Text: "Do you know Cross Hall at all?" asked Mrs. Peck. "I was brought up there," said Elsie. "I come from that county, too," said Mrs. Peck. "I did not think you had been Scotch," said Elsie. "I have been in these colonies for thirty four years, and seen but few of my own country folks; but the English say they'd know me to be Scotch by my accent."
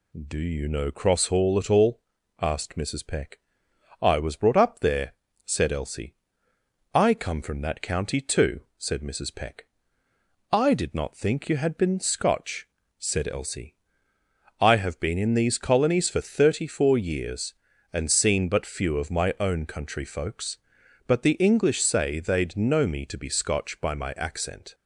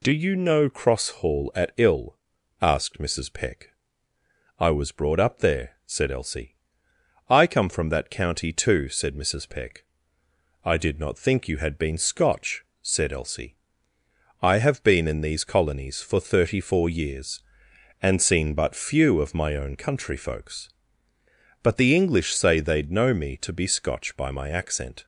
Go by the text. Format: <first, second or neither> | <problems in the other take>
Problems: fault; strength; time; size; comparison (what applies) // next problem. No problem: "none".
first | says "ill" for "all"; at 1.7 s